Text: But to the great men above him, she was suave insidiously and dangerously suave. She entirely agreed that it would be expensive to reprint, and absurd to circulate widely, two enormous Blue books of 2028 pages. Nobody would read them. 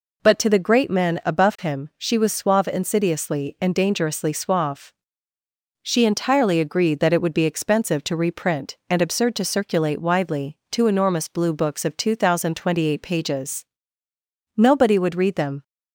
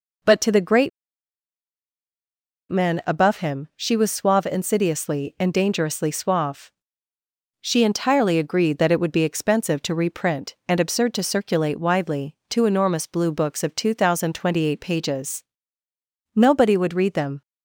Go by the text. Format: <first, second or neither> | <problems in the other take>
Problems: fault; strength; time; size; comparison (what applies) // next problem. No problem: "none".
first | pauses between "great" and "men"; strong; at 0.8 s; 1.8 s long